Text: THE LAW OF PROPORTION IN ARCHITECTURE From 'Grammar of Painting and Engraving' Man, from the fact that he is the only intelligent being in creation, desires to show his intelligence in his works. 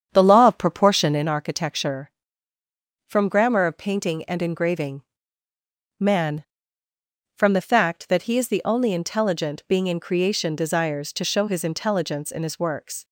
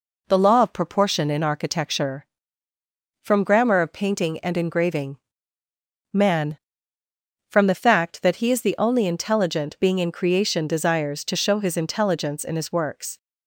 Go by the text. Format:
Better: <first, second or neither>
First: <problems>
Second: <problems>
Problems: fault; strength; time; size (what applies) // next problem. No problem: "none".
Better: second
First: starts louder than the rest; strong; until 1.3 s; 8 dB // pauses between "Engraving" and "Man"; noticeable; at 5.0 s; 0.96 s long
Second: pauses between "Engraving" and "Man"; noticeable; at 5.1 s; 0.94 s long